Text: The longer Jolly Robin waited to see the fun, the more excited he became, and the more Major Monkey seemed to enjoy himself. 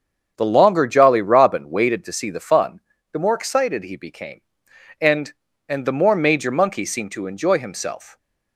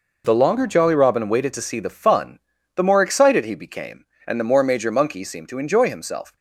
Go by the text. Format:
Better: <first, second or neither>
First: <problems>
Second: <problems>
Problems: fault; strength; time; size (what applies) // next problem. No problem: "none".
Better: second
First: starts louder than the rest; strong; until 1.3 s; 7.5 dB // says "and" twice; at 5.6 s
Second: none